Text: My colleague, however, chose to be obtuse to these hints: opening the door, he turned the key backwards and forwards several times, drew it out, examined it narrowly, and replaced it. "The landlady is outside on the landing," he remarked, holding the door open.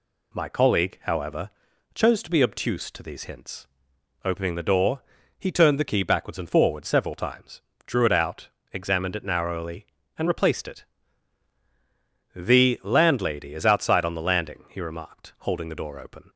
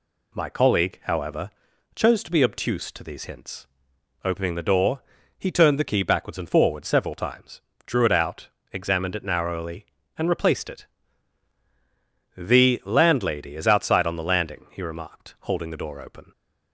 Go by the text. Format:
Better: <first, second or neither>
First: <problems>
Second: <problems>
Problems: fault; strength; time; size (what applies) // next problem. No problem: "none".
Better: neither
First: none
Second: none